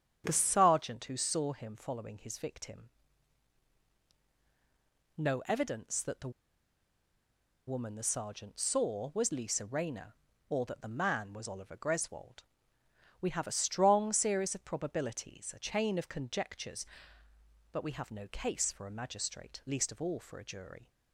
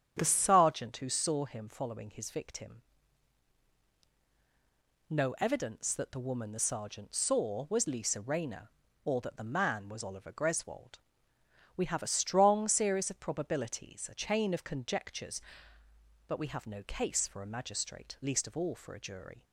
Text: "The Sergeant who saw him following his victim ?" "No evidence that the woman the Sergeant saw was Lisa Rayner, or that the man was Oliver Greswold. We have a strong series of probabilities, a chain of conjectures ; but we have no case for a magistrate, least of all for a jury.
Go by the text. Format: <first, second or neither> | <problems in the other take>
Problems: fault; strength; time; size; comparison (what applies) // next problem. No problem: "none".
second | starts louder than the rest; strong; until 1.2 s; 9.5 dB; strong in the second // pauses between "the" and "woman"; strong; at 6.3 s; 1.3 s long